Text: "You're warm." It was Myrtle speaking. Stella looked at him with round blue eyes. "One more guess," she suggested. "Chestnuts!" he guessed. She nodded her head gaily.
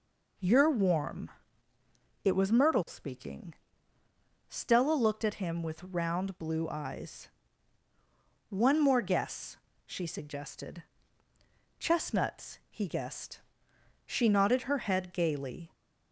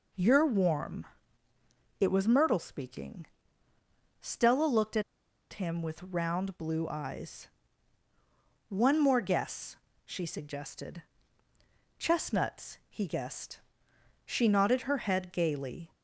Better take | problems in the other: first | pauses between "at" and "him"; noticeable; at 5.0 s; 0.50 s long

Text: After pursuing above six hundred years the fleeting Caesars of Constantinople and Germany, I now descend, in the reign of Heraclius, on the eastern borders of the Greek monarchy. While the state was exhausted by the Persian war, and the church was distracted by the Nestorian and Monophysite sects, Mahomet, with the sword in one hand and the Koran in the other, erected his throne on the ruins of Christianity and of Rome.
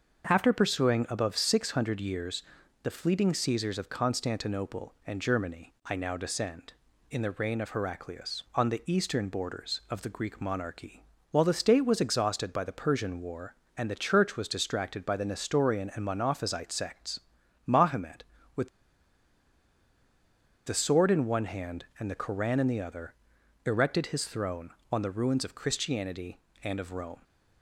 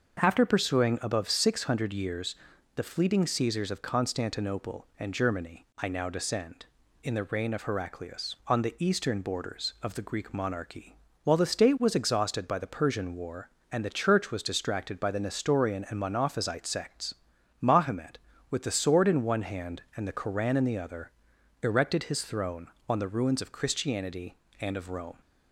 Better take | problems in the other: second | starts louder than the rest; until 1.3 s; 6.5 dB; also in the second // pauses between "years" and "the"; at 2.4 s; 0.40 s long; also in the second // pauses between "with" and "the"; strong; at 18.6 s; 1.9 s long

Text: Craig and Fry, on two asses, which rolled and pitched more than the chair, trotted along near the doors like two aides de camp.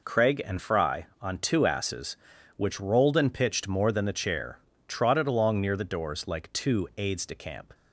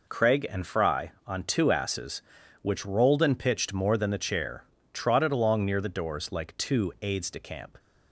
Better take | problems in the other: neither | none

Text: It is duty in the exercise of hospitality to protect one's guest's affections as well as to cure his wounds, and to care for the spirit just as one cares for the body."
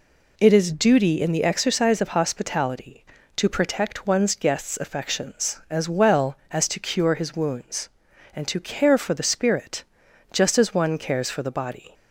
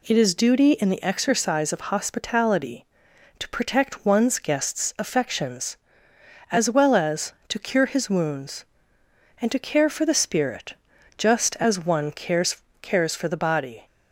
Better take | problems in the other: first | pauses between "spirit" and "just"; at 10.7 s; 0.42 s long; noticeable in the first // says "cares" twice; at 12.8 s

